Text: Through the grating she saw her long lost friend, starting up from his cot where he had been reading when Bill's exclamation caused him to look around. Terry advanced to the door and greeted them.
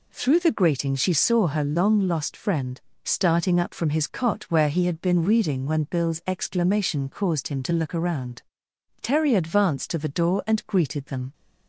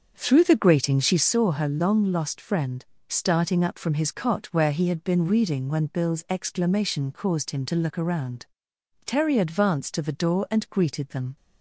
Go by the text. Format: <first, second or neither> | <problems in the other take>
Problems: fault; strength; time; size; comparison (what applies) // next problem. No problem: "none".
first | starts louder than the rest; until 1.4 s; 7 dB